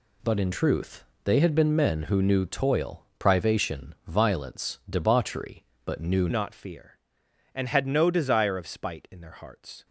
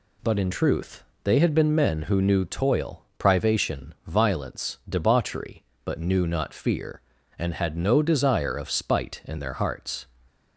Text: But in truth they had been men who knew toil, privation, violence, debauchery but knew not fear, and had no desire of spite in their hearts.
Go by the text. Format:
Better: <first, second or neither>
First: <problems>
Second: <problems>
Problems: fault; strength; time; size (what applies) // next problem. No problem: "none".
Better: second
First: pauses between "truth" and "they"; slight; at 1.0 s; 0.20 s long // changes voice at "not"; from 6.2 s on; 3.6 s long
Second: pauses between "truth" and "they"; slight; at 1.0 s; 0.20 s long